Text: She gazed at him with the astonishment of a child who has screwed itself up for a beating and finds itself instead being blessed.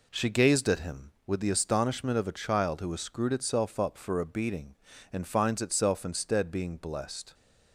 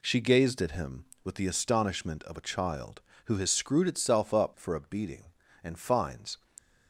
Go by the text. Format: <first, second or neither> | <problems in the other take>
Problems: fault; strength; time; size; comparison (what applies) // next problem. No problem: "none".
first | stops before "itself instead being blessed"; at 6.5 s